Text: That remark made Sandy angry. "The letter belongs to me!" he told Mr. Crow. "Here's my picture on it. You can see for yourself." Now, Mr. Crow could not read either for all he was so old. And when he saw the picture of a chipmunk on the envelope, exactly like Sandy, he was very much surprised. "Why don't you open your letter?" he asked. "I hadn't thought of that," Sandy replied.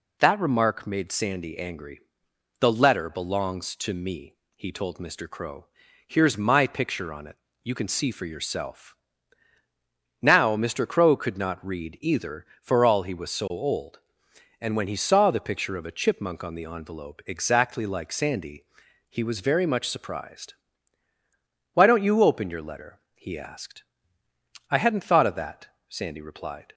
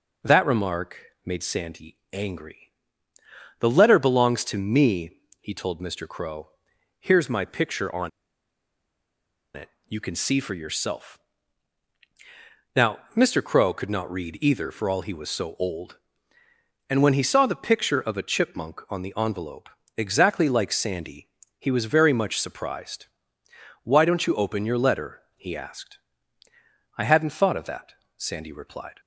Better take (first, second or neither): first